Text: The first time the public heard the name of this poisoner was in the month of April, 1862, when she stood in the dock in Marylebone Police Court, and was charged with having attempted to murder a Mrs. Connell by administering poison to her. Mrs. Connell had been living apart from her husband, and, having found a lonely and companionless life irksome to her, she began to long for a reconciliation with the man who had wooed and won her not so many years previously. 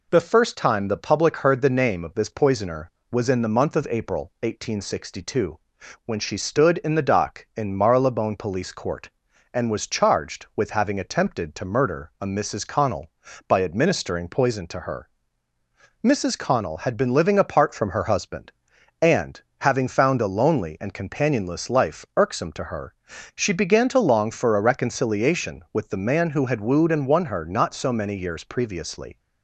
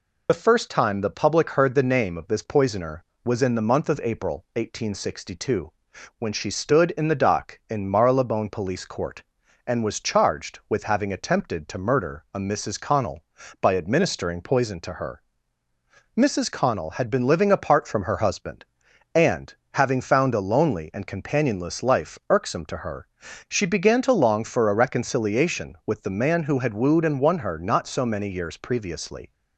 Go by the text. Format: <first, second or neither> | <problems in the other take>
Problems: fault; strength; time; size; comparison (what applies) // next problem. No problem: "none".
first | loses the start of "The"; at 0.2 s; 60 ms